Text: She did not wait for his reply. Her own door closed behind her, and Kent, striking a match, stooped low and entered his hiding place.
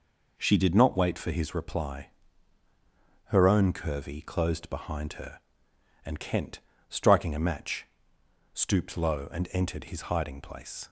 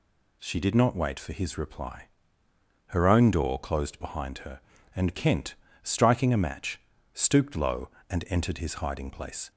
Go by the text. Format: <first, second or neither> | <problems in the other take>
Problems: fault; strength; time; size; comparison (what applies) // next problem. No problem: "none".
second | says "curvy" for "door"; at 3.7 s